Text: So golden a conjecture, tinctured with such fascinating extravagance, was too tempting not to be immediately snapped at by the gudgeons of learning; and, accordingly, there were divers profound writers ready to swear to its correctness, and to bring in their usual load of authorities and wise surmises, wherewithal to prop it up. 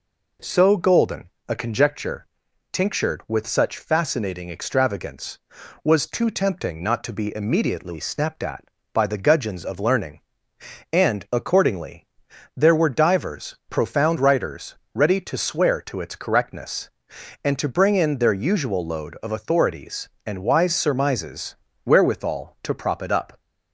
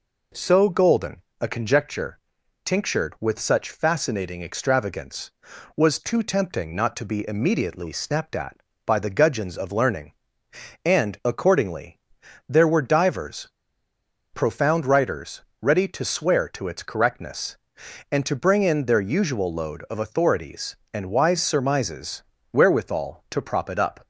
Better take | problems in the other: first | pauses between "golden" and "a"; slight; at 1.2 s; 0.20 s long; slight in the first // pauses between "divers" and "profound"; noticeable; at 13.4 s; 0.84 s long // pauses between "writers" and "ready"; slight; at 15.4 s; 0.18 s long; slight in the first

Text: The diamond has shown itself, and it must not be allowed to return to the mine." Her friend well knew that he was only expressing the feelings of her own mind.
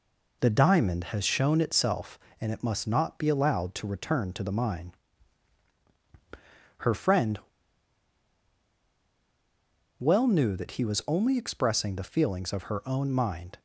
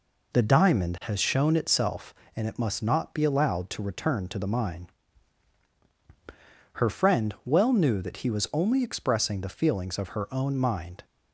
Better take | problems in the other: second | pauses between "friend" and "well"; strong; at 7.3 s; 2.6 s long

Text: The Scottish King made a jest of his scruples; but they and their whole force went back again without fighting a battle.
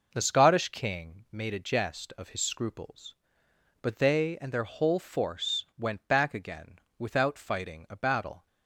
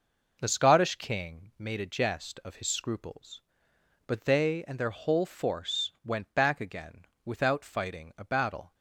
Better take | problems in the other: neither | pauses between "again" and "without"; slight; the same in both

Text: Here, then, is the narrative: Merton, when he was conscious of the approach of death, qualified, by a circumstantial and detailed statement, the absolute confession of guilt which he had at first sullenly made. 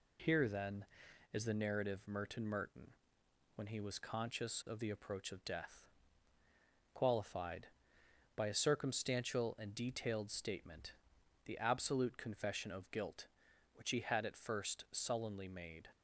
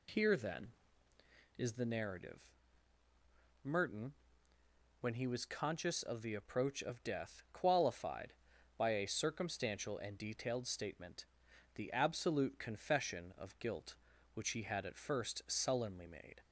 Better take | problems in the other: second | says "Merton" twice; at 2.4 s

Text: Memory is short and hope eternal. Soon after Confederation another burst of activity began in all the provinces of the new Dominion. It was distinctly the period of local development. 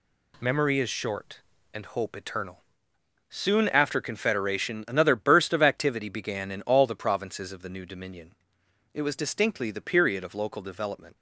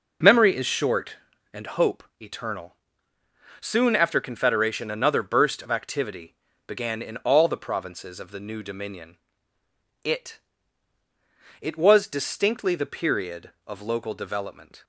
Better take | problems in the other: first | pauses between "hope" and "eternal"; slight; at 2.0 s; 0.18 s long // pauses between "activity" and "began"; slight; at 6.3 s; 0.32 s long // says "It" twice; at 11.5 s

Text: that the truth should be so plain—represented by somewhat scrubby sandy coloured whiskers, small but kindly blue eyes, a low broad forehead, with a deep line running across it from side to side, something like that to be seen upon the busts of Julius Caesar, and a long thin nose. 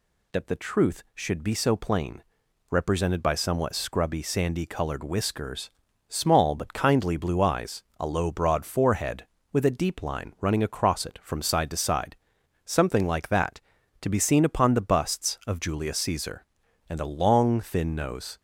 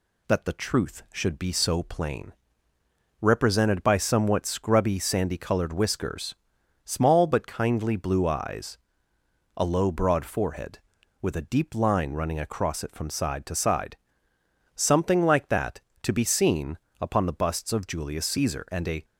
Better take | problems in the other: first | pauses between "seen" and "upon"; slight; at 16.7 s; 0.22 s long // stops before "long thin nose"; at 19.0 s

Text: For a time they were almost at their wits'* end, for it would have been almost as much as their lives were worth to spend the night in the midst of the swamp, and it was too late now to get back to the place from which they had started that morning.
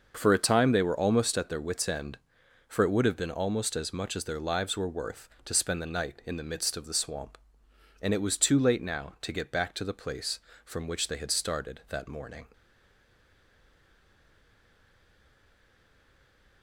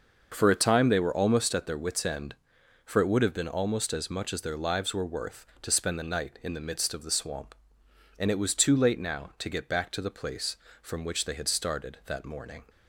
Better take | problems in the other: second | starts louder than the rest; noticeable; until 1.1 s; 6 dB; noticeable in the second // stays silent after the last word; strong; from 12.5 s on; 4.1 s long

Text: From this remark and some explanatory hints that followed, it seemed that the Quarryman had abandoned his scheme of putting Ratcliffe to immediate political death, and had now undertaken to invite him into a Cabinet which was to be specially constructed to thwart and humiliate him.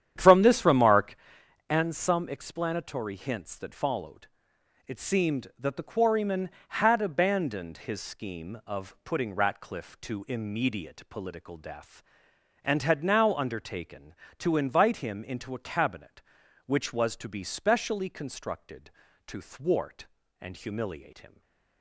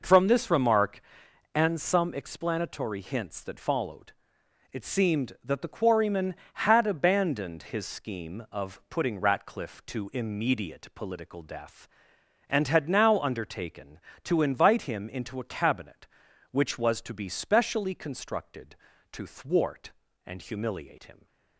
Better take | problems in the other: second | starts louder than the rest; strong; until 1.2 s; 9.5 dB // stays silent after the last word; slight; from 21.2 s on; 0.6 s long

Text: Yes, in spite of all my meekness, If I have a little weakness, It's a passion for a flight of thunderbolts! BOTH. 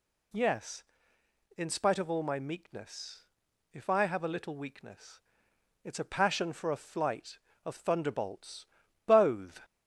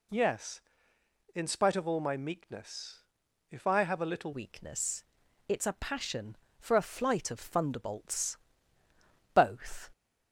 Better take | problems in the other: first | changes voice at "weakness"; from 4.3 s on; 5.6 s long

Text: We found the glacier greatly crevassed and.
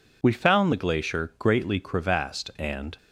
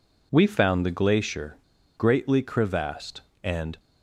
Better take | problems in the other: first | pauses between "glacier" and "greatly"; at 1.5 s; 0.40 s long

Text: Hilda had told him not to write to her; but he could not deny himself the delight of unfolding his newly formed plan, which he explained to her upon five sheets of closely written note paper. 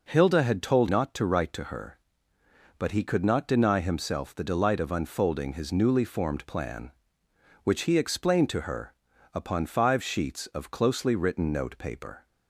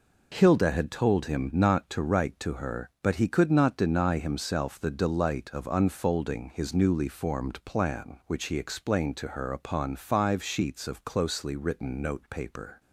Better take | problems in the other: second | skips "him"; at 0.8 s // pauses between "her" and "upon"; at 8.9 s; 0.38 s long

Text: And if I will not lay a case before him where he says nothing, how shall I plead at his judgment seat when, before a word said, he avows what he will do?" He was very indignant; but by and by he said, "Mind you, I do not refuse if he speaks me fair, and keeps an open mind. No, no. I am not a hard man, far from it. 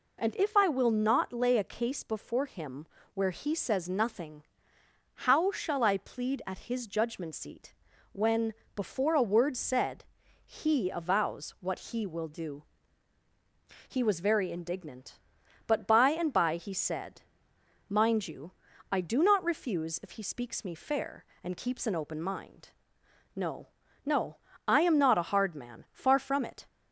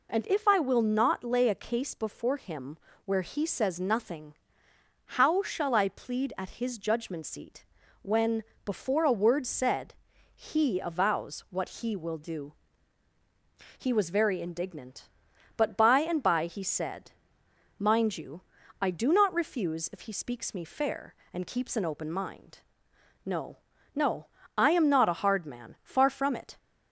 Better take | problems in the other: neither | pauses between "him" and "where"; slight; the same in both // pauses between "seat" and "when"; the same in both

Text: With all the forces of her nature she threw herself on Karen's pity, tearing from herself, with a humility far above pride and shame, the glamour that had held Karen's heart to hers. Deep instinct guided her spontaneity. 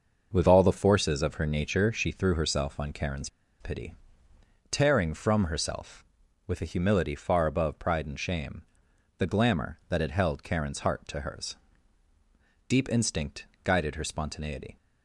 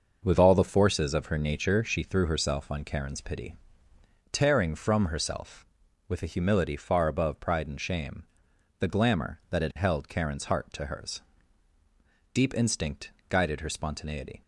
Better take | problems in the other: second | starts louder than the rest; noticeable; until 1.3 s; 6 dB; noticeable in the second // pauses between "Karen's" and "pity"; slight; at 3.2 s; 0.32 s long // pauses between "instinct" and "guided"; slight; at 13.4 s; 0.18 s long; slight in the second

